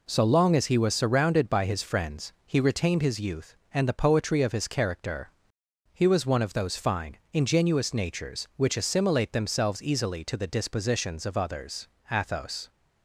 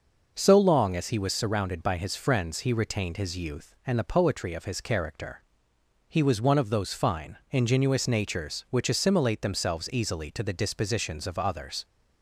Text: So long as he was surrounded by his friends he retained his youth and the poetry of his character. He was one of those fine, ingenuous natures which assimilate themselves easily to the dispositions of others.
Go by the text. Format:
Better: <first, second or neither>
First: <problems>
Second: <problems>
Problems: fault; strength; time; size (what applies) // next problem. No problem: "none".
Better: second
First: goes on to say "Athos"; from 12.0 s on; 0.60 s long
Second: none